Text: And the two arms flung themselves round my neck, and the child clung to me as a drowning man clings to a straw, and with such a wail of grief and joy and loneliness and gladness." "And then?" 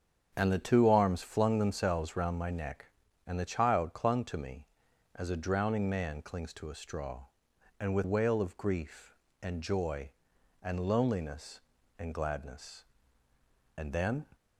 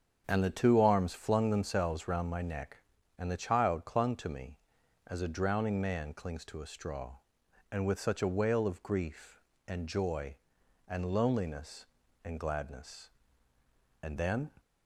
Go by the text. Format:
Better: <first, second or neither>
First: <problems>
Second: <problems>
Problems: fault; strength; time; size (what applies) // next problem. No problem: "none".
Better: second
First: starts louder than the rest; strong; until 1.3 s; 7.5 dB // skips "such a"; at 8.0 s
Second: starts louder than the rest; strong; until 1.2 s; 7.5 dB